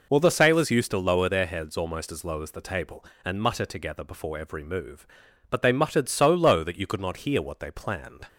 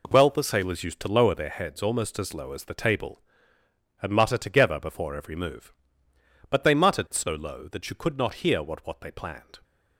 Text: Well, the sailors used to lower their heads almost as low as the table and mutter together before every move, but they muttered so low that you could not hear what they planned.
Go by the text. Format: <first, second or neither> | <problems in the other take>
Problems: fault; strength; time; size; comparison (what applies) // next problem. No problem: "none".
first | says "what" twice; at 8.8 s